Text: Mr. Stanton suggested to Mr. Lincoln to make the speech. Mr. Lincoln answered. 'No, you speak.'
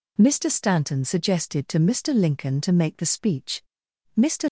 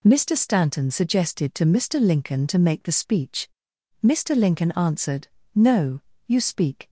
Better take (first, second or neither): second